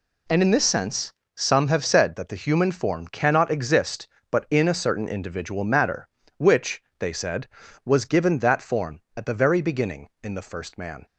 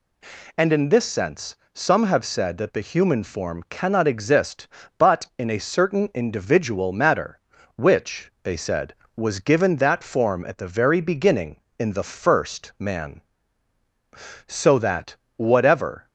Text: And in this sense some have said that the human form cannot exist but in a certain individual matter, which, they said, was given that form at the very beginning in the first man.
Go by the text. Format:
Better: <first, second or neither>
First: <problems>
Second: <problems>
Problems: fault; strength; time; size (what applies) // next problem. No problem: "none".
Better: first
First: pauses between "sense" and "some"; slight; at 1.1 s; 0.24 s long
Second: pauses between "sense" and "some"; slight; at 1.5 s; 0.18 s long // goes on to say "So that whatever"; from 14.4 s on; 1.6 s long